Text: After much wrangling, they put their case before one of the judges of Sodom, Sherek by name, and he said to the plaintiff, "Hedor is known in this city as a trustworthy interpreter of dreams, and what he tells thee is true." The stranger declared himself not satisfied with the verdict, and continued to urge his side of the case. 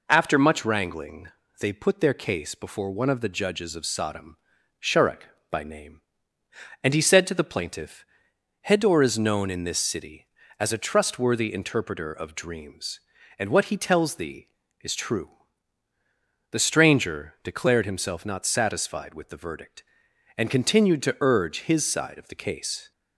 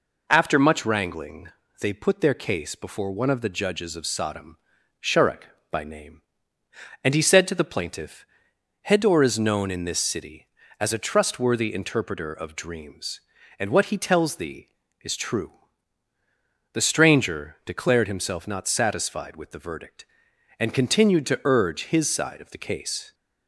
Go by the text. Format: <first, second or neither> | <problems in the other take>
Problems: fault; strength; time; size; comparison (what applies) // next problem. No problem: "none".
neither | none